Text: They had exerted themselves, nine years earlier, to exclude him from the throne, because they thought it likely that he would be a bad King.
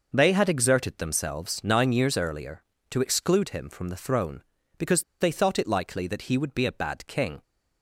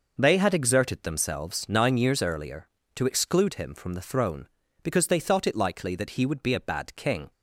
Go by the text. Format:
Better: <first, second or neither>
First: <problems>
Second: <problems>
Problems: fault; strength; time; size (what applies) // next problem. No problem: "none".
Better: second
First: pauses between "because" and "they"; slight; at 5.0 s; 0.18 s long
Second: none